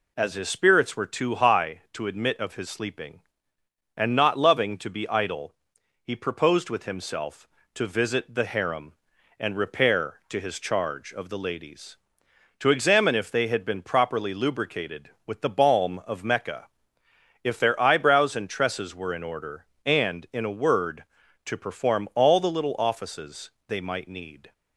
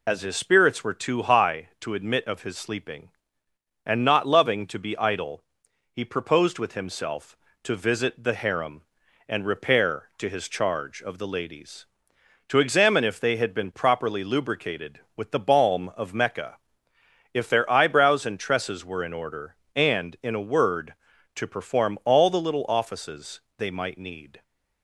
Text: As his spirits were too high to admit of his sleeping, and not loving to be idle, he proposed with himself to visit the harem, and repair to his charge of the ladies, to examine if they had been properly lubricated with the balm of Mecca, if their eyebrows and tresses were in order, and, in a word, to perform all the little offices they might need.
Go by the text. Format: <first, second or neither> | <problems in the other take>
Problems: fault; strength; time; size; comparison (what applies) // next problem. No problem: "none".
first | loses the start of "As"; at 0.0 s; 40 ms // pauses between "offices" and "they"; slight; at 23.3 s; 0.20 s long; slight in the first